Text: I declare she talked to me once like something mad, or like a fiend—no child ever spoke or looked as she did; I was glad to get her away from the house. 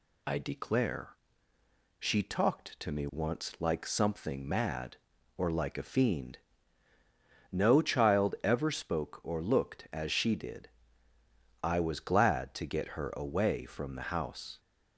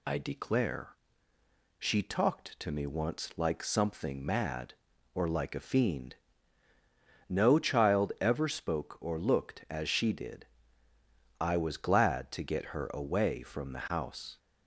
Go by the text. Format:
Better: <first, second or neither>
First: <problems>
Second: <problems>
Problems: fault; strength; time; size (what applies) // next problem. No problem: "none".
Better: neither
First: pauses between "declare" and "she"; noticeable; at 1.1 s; 0.82 s long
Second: pauses between "declare" and "she"; noticeable; at 0.9 s; 0.82 s long